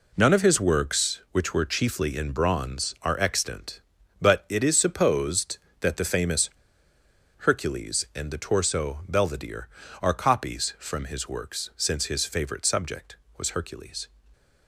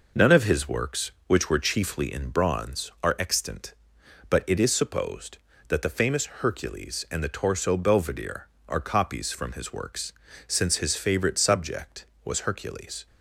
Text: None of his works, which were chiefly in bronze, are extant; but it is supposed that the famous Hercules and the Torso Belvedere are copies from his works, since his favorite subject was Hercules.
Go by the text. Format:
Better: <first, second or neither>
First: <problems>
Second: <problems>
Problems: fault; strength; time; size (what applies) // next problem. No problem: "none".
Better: second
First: pauses between "famous" and "Hercules"; noticeable; at 6.4 s; 0.86 s long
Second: none